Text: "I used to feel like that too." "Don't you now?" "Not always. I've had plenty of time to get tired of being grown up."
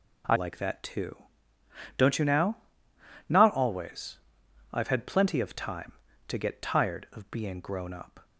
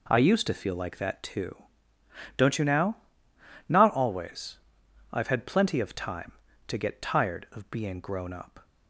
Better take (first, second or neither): second